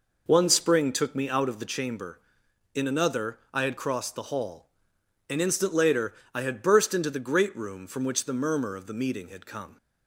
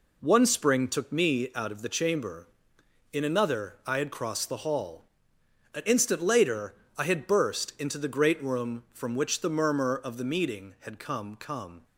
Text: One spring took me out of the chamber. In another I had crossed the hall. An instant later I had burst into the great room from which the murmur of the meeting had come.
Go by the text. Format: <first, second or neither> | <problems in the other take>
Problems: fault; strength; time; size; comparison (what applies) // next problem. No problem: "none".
first | pauses between "later" and "I"; slight; at 6.7 s; 0.20 s long; slight in the first // says "come" twice; at 11.3 s